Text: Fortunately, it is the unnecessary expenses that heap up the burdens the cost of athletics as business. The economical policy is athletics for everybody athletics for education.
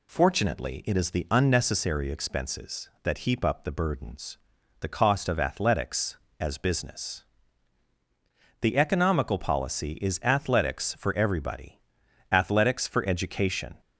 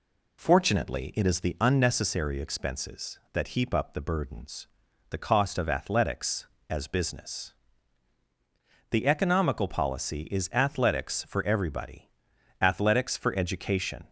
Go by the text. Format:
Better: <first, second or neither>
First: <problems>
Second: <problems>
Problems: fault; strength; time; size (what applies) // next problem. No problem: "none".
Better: first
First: pauses between "burdens" and "the"; at 4.3 s; 0.42 s long // pauses between "everybody" and "athletics"; noticeable; at 11.7 s; 0.54 s long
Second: starts louder than the rest; slight; until 1.6 s; 2.5 dB // pauses between "burdens" and "the"; at 4.6 s; 0.42 s long // pauses between "everybody" and "athletics"; noticeable; at 12.0 s; 0.54 s long